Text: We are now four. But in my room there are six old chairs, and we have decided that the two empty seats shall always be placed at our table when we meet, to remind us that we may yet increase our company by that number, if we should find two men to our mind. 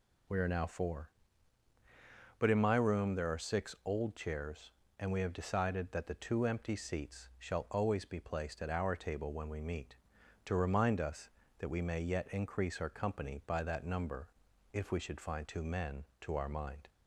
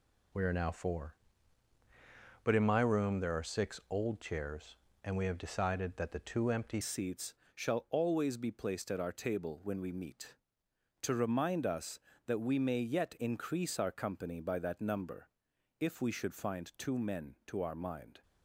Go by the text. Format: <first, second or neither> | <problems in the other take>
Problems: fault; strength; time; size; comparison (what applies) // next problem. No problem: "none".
first | changes voice at "seats"; from 6.8 s on; 11.4 s long // pauses between "seats" and "shall"; slight; at 7.3 s; 0.20 s long